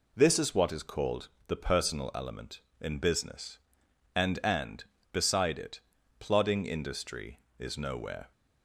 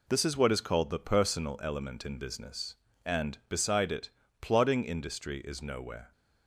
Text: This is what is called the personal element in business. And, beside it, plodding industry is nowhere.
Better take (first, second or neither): second